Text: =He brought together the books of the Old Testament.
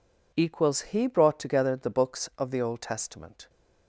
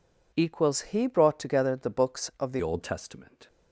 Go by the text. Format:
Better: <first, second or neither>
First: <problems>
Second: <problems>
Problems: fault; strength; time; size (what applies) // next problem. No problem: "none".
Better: first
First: none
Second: changes voice at "Old"; from 2.6 s on; 0.8 s long